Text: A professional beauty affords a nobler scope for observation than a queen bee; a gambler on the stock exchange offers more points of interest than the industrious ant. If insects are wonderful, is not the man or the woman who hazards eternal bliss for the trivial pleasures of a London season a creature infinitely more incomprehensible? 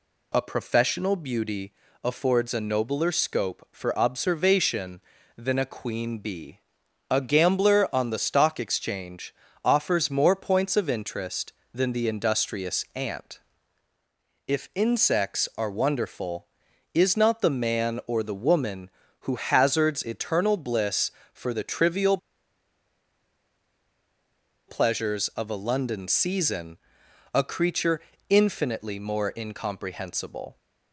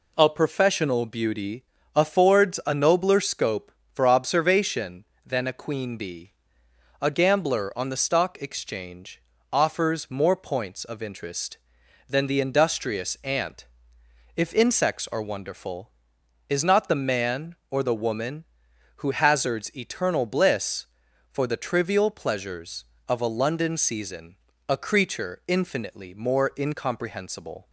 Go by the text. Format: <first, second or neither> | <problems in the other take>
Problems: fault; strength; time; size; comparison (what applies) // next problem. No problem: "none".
second | pauses between "beauty" and "affords"; slight; at 1.7 s; 0.30 s long; slight in the second // pauses between "exchange" and "offers"; slight; at 9.3 s; 0.32 s long; slight in the second // pauses between "trivial" and "pleasures"; strong; at 22.1 s; 2.5 s long // pauses between "season" and "a"; noticeable; at 26.7 s; 0.52 s long; slight in the second // pauses between "creature" and "infinitely"; slight; at 28.0 s; 0.30 s long